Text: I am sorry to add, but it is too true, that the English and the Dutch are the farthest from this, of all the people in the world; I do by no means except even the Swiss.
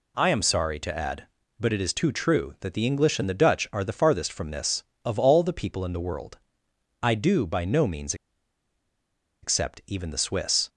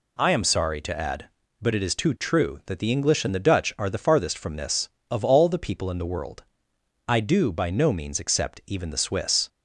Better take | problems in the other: second | pauses between "means" and "except"; strong; at 8.1 s; 1.2 s long

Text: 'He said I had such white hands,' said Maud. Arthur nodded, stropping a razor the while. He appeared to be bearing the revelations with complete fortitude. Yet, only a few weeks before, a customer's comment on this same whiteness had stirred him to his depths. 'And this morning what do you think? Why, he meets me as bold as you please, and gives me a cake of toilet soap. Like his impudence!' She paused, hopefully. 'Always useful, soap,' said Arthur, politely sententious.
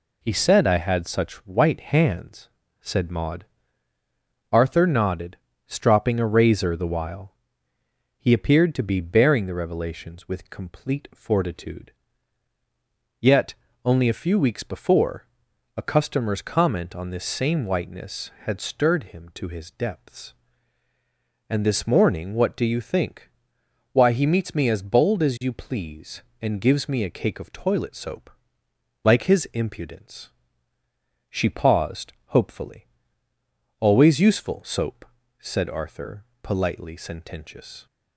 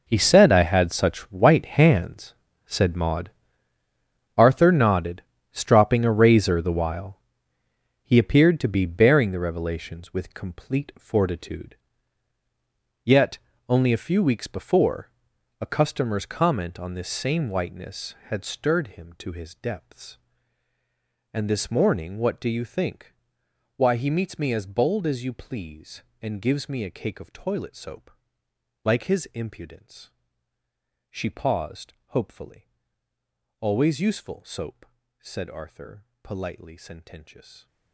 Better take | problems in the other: first | gets quieter; strong; throughout; 15.5 dB

